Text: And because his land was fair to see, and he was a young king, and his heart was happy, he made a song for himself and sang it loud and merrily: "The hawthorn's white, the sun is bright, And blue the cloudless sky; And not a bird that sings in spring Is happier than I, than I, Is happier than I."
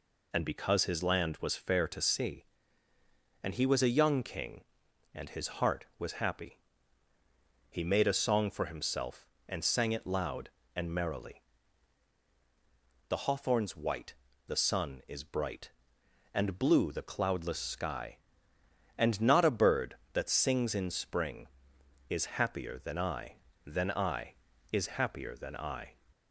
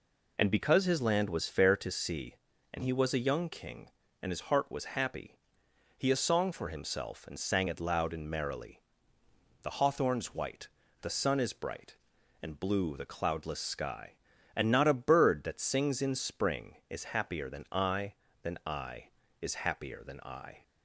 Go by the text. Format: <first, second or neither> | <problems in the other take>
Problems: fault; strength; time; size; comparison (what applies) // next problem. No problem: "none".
first | skips "made"; at 6.1 s